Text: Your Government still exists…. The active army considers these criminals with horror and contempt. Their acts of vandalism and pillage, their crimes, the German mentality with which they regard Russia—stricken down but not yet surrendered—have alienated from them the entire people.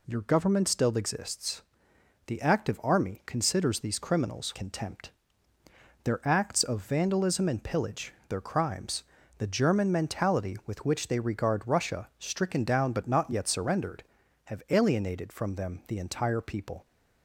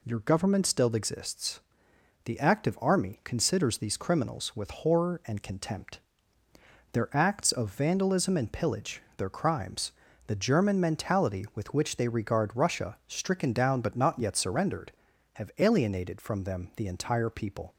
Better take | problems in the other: second | skips "with horror and"; at 4.5 s

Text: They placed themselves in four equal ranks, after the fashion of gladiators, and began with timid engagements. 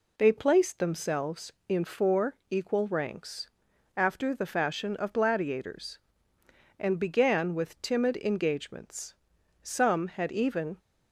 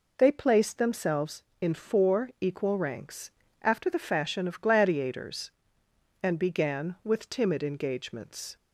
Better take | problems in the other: second | goes on to say "Some had even"; noticeable; from 9.6 s on; 1.1 s long

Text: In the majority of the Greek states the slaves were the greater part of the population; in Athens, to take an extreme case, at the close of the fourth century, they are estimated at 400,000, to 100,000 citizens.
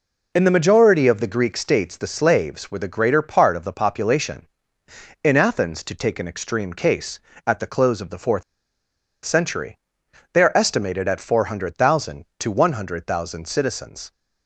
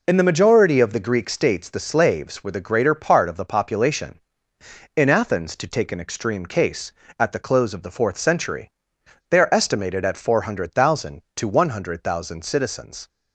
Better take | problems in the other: second | pauses between "fourth" and "century"; noticeable; at 8.4 s; 0.82 s long

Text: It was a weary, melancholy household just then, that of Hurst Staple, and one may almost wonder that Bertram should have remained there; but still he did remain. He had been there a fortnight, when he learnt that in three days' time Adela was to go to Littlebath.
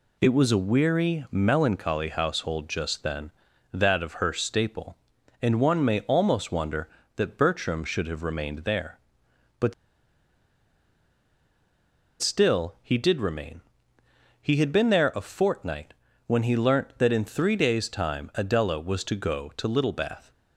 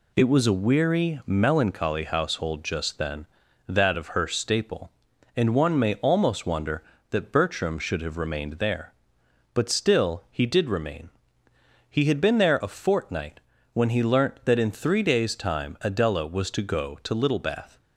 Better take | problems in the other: second | pauses between "but" and "still"; strong; at 9.7 s; 2.4 s long

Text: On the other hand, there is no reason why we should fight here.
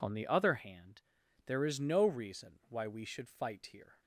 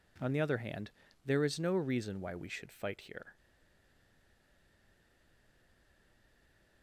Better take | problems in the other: first | stays silent after the last word; strong; from 3.3 s on; 3.5 s long

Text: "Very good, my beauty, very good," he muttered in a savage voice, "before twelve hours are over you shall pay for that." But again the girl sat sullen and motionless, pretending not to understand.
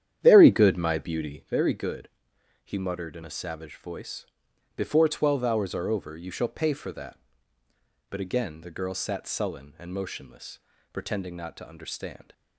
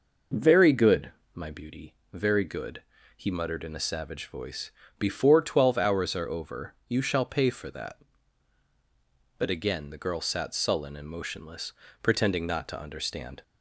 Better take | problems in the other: second | starts louder than the rest; strong; until 1.5 s; 10 dB

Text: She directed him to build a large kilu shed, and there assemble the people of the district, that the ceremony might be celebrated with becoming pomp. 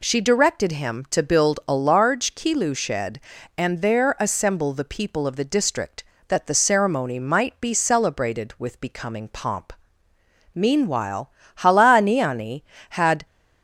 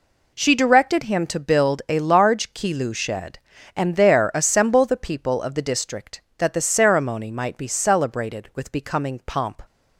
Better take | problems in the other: second | goes on to say "Meanwhile Halaaniani had"; strong; from 10.5 s on; 2.7 s long

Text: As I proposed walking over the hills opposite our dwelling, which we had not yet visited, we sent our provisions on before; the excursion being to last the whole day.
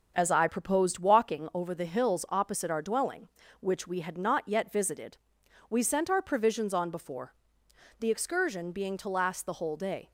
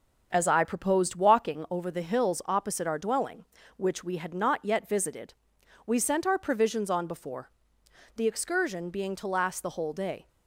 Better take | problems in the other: neither | starts louder than the rest; the same in both

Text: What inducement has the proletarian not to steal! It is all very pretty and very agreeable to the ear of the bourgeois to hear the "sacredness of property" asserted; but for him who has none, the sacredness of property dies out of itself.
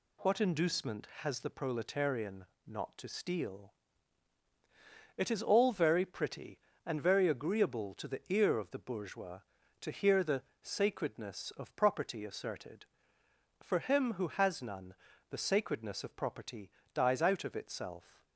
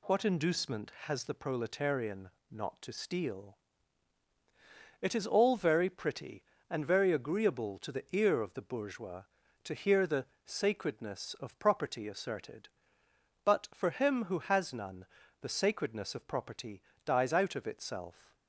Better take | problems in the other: second | pauses between "proletarian" and "not"; slight; at 2.4 s; 0.24 s long; slight in the second // pauses between "the" and "sacredness"; slight; at 10.4 s; 0.20 s long; slight in the second // skips "but"; at 13.2 s // pauses between "property" and "dies"; slight; at 16.6 s; 0.24 s long; slight in the second

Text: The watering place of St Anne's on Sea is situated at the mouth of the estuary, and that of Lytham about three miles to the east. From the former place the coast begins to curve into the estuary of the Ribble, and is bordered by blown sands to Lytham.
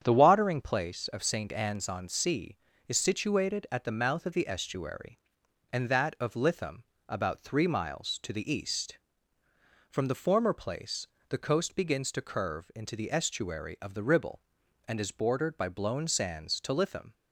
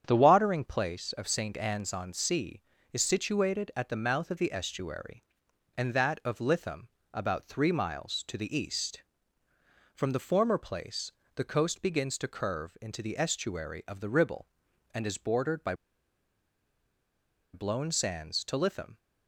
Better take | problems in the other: first | starts louder than the rest; strong; until 1.0 s; 8.5 dB; strong in the first // pauses between "Lytham" and "about"; slight; at 6.8 s; 0.22 s long; slight in the first // pauses between "place" and "the"; slight; at 11.1 s; 0.22 s long; slight in the first // pauses between "by" and "blown"; strong; at 15.7 s; 1.8 s long

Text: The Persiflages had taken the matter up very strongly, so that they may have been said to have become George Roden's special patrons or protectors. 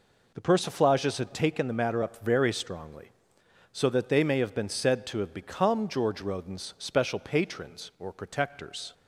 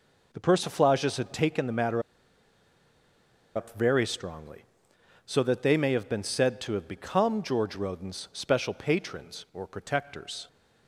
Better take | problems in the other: first | pauses between "matter" and "up"; strong; at 2.0 s; 1.5 s long

